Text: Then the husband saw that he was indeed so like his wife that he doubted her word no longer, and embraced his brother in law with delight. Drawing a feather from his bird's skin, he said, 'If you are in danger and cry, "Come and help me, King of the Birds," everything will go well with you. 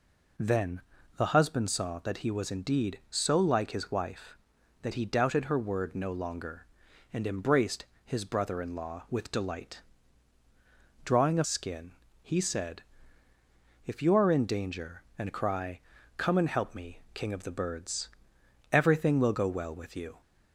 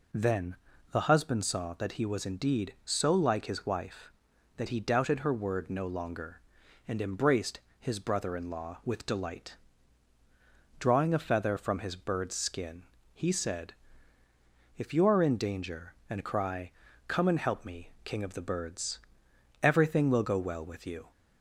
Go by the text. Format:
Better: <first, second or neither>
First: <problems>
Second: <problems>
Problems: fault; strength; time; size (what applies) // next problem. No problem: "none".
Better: second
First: pauses between "Then" and "the"; slight; at 0.8 s; 0.36 s long // pauses between "embraced" and "his"; slight; at 7.8 s; 0.20 s long // skips "feather from his bird's"; at 11.4 s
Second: pauses between "Then" and "the"; slight; at 0.5 s; 0.36 s long // pauses between "embraced" and "his"; slight; at 7.5 s; 0.20 s long